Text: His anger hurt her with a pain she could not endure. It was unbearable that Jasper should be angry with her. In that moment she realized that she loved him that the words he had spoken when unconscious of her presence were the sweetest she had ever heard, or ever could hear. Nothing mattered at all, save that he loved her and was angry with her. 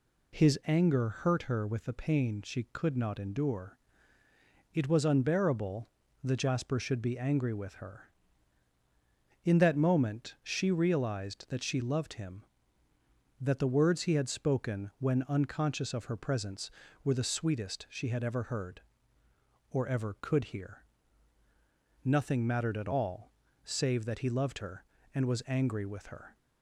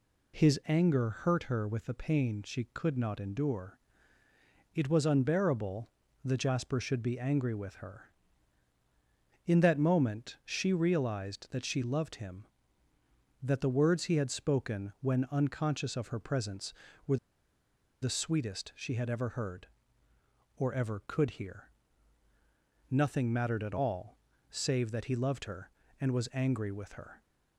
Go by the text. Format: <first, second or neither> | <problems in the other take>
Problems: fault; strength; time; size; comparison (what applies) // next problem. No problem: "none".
first | pauses between "were" and "the"; noticeable; at 17.1 s; 0.85 s long